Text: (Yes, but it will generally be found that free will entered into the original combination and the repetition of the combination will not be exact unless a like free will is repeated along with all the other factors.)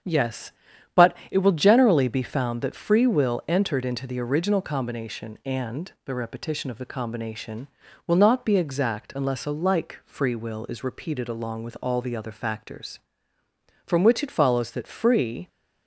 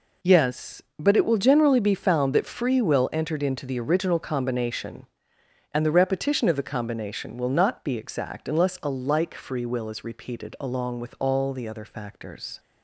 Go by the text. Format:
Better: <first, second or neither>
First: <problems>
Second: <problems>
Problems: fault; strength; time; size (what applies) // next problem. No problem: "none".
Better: second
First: starts louder than the rest; strong; until 1.6 s; 7.5 dB // goes on to say "From which it follows that free"; from 13.8 s on; 1.6 s long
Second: none